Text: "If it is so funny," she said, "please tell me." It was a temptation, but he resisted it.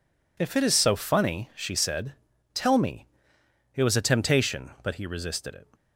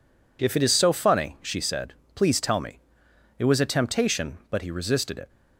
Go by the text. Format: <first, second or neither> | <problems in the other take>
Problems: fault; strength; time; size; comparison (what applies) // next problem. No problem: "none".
second | skips "please"; at 2.3 s